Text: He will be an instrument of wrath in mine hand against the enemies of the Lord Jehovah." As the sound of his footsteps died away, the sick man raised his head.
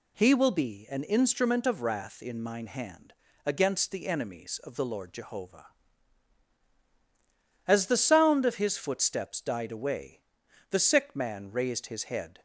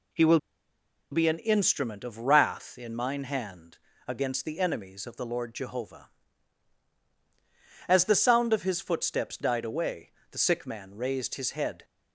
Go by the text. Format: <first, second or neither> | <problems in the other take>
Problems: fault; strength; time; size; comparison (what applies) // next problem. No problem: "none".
first | pauses between "will" and "be"; noticeable; at 0.3 s; 0.73 s long // pauses between "hand" and "against"; slight; at 3.7 s; 0.28 s long; slight in the first